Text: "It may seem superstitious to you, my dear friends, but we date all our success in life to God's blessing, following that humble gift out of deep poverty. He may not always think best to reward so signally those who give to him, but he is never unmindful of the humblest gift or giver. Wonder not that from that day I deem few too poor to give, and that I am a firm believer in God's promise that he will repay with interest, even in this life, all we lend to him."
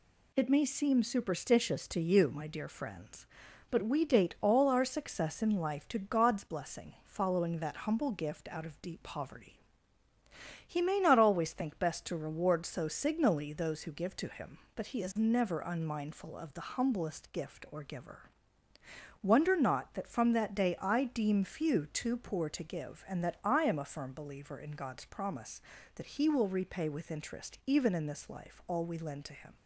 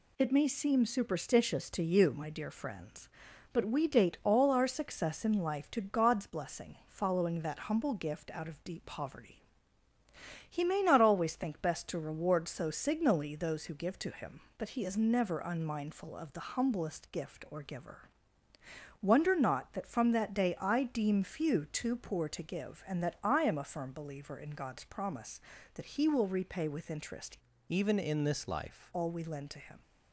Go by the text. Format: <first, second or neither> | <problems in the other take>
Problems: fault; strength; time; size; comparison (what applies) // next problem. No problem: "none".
first | changes voice from "even" to "life"; from 27.6 to 28.9 s; 1.3 s long